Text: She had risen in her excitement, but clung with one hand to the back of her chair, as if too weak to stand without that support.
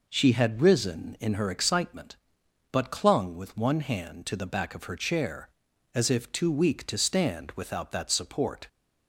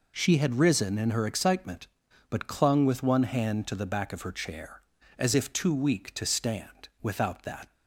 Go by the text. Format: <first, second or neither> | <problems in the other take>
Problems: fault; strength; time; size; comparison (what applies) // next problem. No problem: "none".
first | stops before "support"; at 7.7 s